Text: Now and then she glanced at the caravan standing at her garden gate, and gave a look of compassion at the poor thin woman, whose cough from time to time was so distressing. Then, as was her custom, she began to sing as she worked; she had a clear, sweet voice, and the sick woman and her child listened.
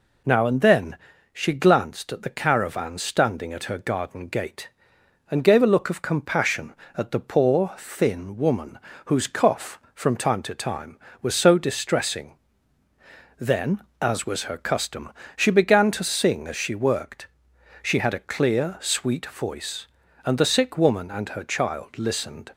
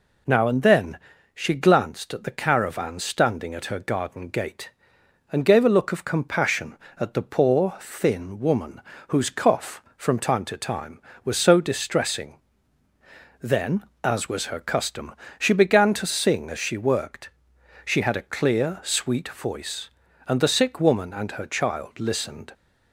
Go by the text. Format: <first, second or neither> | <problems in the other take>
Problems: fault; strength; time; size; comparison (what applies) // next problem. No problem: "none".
neither | pauses between "then" and "she"; slight; the same in both